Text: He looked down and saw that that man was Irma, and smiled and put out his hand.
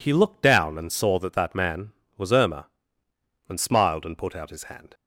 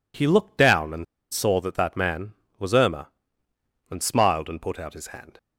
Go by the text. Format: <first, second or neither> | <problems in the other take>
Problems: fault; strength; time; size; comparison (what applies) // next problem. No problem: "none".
first | pauses between "and" and "saw"; slight; at 1.0 s; 0.26 s long